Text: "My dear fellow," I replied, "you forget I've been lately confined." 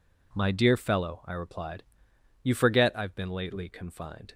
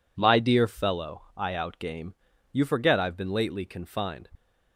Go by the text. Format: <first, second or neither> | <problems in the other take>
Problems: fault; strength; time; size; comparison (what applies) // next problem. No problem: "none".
first | says "outgame" for "replied"; at 1.5 s